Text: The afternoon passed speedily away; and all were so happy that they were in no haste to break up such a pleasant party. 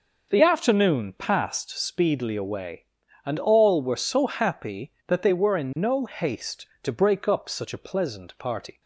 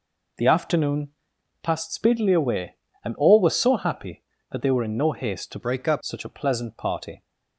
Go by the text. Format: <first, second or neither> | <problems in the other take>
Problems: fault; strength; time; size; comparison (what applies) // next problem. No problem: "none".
first | pauses between "afternoon" and "passed"; noticeable; at 1.0 s; 0.52 s long // changes voice from "break" to "up"; from 5.6 to 6.0 s; 0.4 s long